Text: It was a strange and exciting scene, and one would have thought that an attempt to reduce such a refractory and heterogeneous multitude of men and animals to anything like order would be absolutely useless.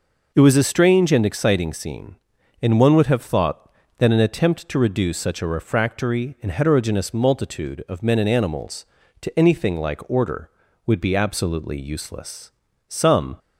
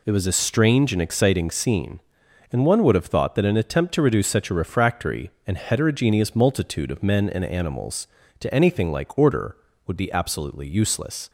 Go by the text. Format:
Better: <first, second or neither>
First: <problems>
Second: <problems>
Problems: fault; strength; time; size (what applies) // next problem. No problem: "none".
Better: second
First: goes on to say "Some"; from 12.8 s on; 0.50 s long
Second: none